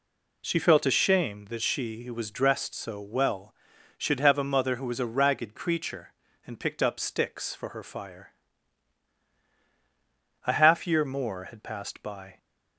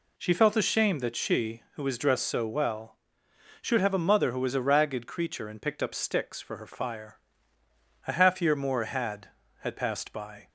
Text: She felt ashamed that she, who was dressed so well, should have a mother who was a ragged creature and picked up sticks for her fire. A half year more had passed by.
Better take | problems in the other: first | says "had" twice; at 9.5 s

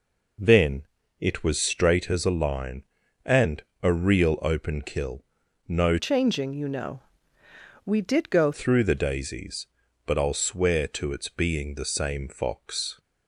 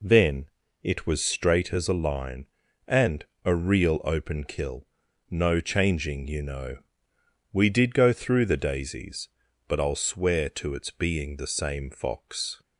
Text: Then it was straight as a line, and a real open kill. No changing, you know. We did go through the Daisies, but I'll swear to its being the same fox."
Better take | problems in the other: second | pauses between "Then" and "it"; slight; at 0.8 s; 0.36 s long; slight in the second // pauses between "and" and "a"; slight; at 3.6 s; 0.22 s long; slight in the second // changes voice from "changing" to "go"; from 5.9 to 8.5 s; 2.6 s long

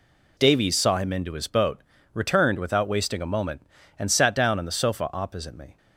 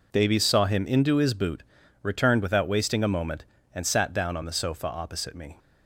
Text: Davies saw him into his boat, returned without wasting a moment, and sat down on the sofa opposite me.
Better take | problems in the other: first | says "boot" for "boat"; at 1.3 s

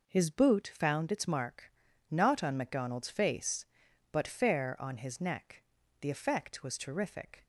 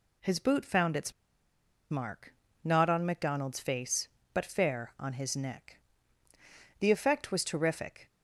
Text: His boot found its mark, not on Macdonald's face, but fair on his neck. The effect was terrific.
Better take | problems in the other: first | pauses between "its" and "mark"; noticeable; at 1.1 s; 0.79 s long

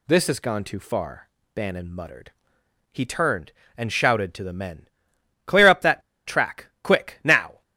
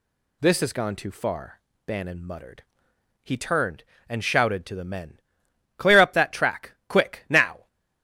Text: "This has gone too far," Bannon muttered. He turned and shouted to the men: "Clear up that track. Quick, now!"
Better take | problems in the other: second | pauses between "that" and "track"; slight; at 6.0 s; 0.25 s long

